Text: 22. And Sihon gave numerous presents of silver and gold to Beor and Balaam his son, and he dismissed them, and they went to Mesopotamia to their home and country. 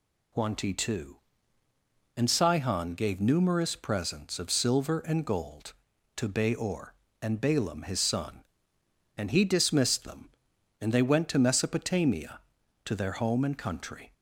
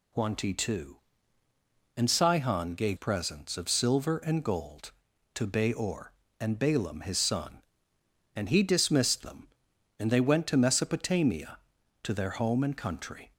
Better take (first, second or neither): first